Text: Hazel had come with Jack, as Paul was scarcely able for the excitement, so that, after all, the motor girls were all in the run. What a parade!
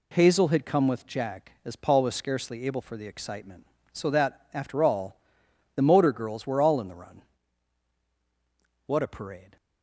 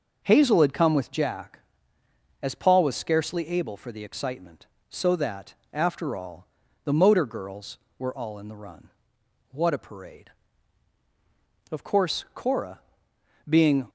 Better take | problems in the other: first | goes on to say "Of course Cora being"; strong; from 11.6 s on; 2.1 s long

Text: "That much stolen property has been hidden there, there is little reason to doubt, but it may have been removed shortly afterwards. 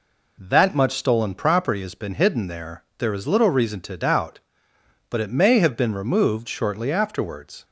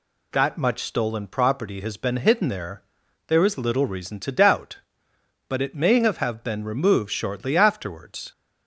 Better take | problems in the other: first | says "have" twice; at 6.1 s

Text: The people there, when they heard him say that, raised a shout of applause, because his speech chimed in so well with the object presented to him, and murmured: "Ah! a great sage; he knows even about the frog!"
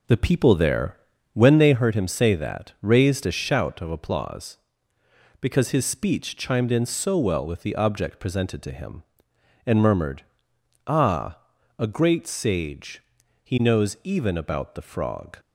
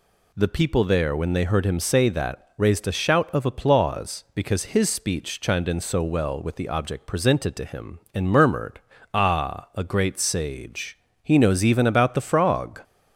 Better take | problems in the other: second | starts louder than the rest; noticeable; until 1.8 s; 5 dB

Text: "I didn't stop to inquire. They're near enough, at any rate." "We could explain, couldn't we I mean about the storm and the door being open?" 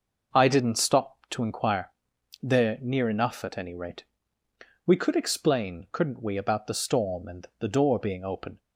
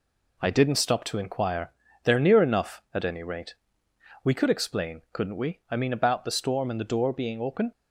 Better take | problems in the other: second | skips "I mean"; at 6.3 s

